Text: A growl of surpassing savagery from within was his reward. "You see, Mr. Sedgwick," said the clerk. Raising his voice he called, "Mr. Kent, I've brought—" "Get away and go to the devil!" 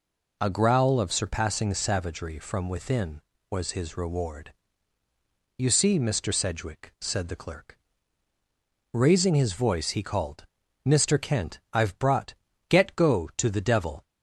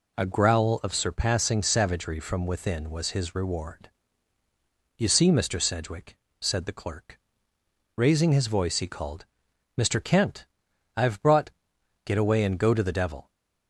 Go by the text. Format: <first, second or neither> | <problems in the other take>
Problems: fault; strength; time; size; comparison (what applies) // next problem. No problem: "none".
second | skips "away and"; at 12.9 s